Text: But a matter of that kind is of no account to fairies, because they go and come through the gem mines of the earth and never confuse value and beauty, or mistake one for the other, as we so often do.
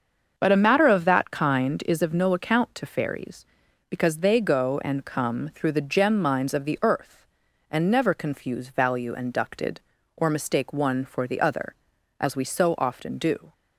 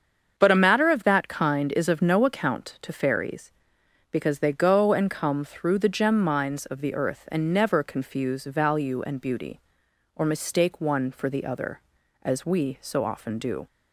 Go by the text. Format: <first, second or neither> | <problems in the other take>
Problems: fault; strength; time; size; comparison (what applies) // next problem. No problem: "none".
second | starts louder than the rest; until 1.3 s; 6.5 dB; also in the second // says "ducted" for "beauty"; at 9.3 s